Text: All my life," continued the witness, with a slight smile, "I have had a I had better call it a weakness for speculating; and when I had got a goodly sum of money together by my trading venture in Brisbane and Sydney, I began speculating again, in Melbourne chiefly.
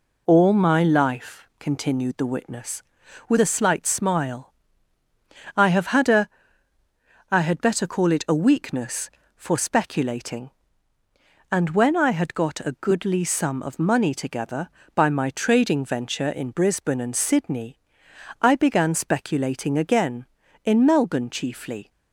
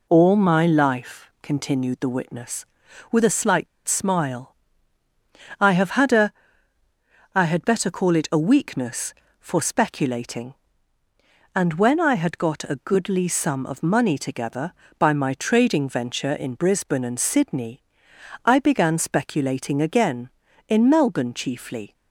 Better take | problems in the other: first | pauses between "a" and "slight"; slight; at 3.6 s; 0.20 s long // pauses between "a" and "I"; at 6.3 s; 1.0 s long; also in the first

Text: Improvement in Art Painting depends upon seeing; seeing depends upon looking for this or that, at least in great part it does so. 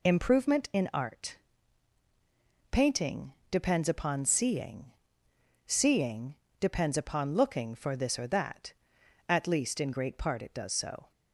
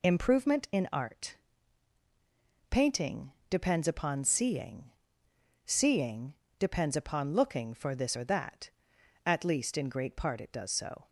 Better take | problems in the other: neither | pauses between "Art" and "Painting"; strong; the same in both // pauses between "Painting" and "depends"; slight; the same in both // pauses between "seeing" and "depends"; slight; the same in both

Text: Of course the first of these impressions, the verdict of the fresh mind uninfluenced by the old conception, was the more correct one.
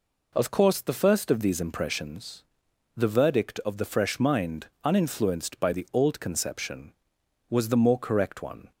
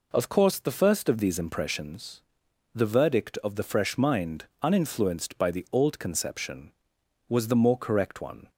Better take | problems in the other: neither | pauses between "mind" and "uninfluenced"; slight; the same in both

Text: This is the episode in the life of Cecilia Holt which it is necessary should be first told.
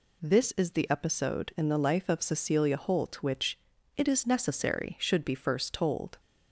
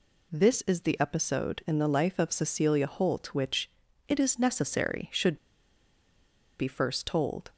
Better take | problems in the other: first | pauses between "which" and "it"; at 3.7 s; 0.38 s long; also in the first // pauses between "should" and "be"; at 5.3 s; 1.2 s long

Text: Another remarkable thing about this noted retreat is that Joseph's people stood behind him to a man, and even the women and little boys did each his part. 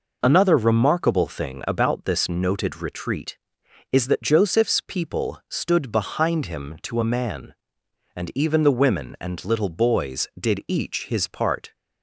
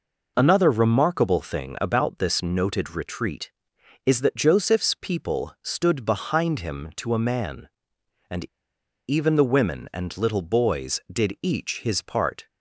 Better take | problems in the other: first | pauses between "and" and "even"; noticeable; at 8.4 s; 0.62 s long

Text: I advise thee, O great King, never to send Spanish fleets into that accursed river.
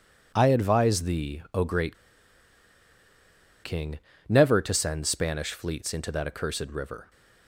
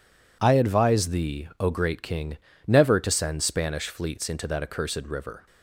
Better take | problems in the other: second | pauses between "great" and "King"; strong; at 1.9 s; 1.6 s long

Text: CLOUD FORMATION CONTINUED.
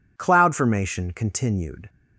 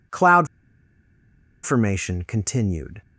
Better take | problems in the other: first | pauses between "CLOUD" and "FORMATION"; at 0.4 s; 1.1 s long

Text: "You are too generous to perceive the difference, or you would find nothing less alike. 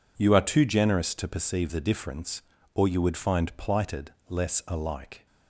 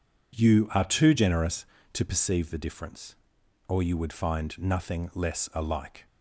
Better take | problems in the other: second | says "plighted" for "nothing"; at 3.5 s

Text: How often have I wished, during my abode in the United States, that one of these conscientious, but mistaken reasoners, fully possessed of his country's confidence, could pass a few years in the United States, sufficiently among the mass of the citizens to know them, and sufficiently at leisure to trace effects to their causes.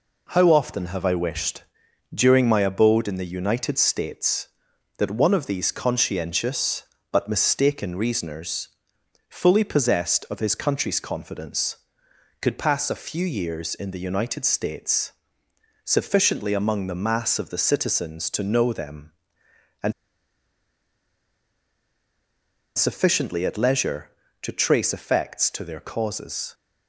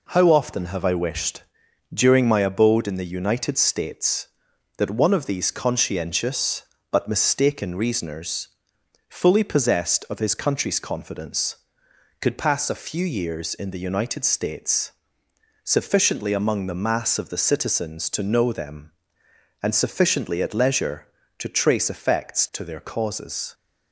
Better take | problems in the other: second | pauses between "and" and "sufficiently"; strong; at 19.9 s; 2.8 s long

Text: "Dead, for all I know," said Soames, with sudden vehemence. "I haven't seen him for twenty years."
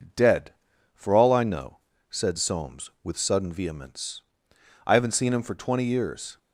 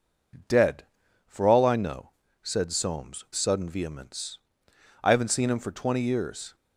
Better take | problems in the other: first | skips "with"; at 3.2 s

